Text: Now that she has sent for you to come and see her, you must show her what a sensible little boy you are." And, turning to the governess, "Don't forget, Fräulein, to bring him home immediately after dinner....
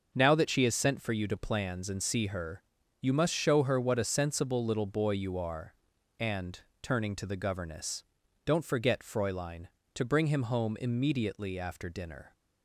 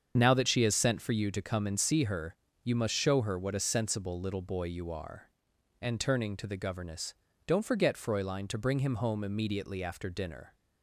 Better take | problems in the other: second | starts louder than the rest; noticeable; until 1.1 s; 6 dB; strong in the second // says "plans" for "come"; at 1.3 s

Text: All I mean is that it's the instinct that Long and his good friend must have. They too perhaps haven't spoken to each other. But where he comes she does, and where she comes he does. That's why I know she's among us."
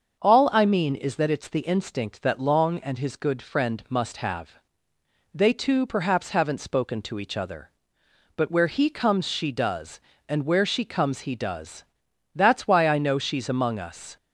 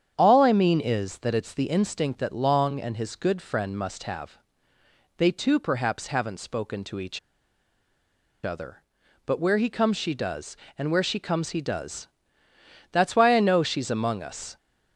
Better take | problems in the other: first | starts louder than the rest; strong; until 1.1 s; 8.5 dB; also in the first // pauses between "each" and "other"; strong; at 7.1 s; 1.2 s long

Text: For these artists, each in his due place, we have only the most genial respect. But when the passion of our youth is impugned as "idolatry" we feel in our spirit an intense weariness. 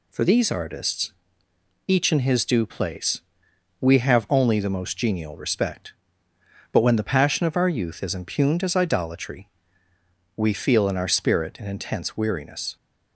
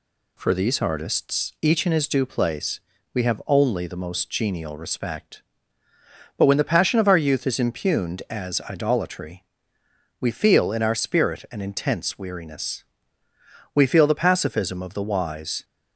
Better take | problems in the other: first | pauses between "idolatry" and "we"; noticeable; at 9.4 s; 0.78 s long; noticeable in the first // goes on to say "We feel the pacifism of the wise"; strong; from 13.7 s on; 1.9 s long

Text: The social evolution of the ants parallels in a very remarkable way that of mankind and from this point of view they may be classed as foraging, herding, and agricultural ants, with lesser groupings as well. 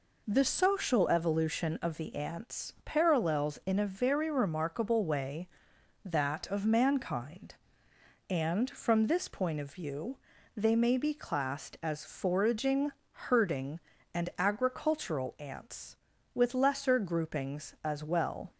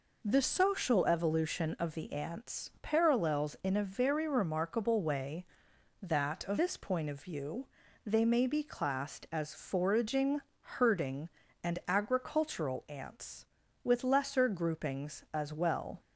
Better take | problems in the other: first | skips "mankind and from"; at 6.5 s // pauses between "view" and "they"; at 7.6 s; 0.38 s long; also in the first

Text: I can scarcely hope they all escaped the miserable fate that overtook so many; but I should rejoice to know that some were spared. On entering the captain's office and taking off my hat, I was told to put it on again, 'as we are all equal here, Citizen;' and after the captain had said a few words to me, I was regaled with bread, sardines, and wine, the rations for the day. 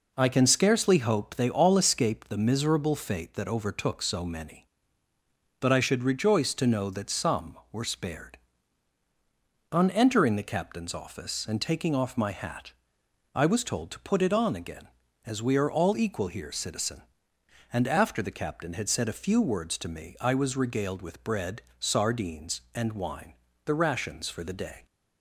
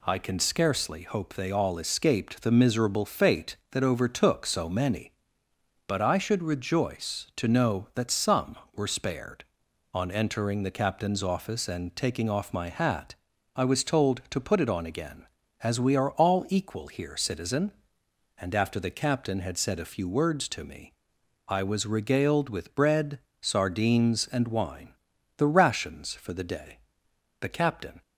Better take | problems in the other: first | goes on to say "The captain"; from 27.4 s on; 0.60 s long

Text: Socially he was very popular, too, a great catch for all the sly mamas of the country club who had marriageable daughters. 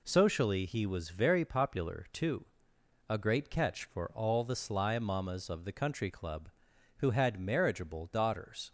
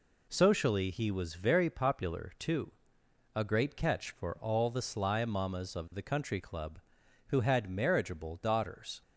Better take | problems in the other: neither | none

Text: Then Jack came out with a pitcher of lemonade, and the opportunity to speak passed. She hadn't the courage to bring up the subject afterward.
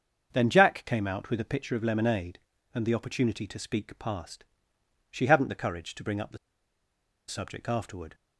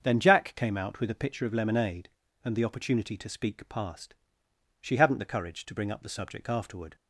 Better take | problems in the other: second | starts louder than the rest; until 1.3 s; 6.5 dB; also in the second // pauses between "the" and "subject"; noticeable; at 6.3 s; 0.90 s long

